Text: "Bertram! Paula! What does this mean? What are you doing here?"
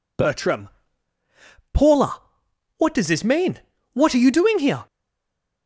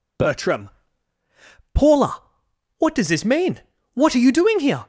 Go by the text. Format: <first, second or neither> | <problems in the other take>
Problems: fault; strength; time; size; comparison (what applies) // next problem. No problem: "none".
second | stays silent after the last word; slight; from 4.8 s on; 0.8 s long